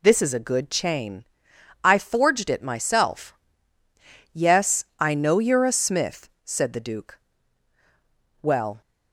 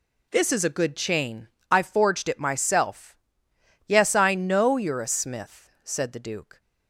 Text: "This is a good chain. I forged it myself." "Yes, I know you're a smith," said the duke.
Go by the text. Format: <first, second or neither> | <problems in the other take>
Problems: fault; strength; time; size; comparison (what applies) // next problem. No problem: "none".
second | goes on to say "Well"; slight; from 8.4 s on; 0.40 s long